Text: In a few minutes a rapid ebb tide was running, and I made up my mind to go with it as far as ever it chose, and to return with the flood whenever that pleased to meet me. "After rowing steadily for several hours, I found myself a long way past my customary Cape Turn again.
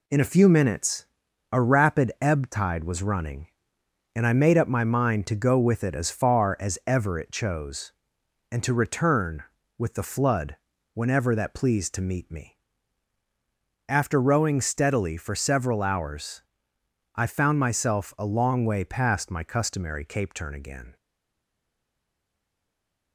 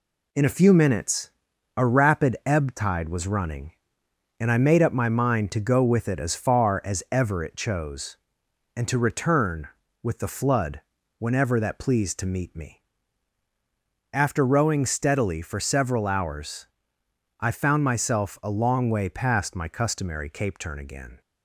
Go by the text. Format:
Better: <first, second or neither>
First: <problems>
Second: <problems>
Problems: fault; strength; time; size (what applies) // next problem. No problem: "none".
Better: second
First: pauses between "minutes" and "a"; noticeable; at 1.0 s; 0.46 s long // pauses between "flood" and "whenever"; slight; at 10.5 s; 0.36 s long // stays silent after the last word; from 20.9 s on; 2.2 s long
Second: pauses between "minutes" and "a"; noticeable; at 1.3 s; 0.46 s long // pauses between "flood" and "whenever"; slight; at 10.8 s; 0.36 s long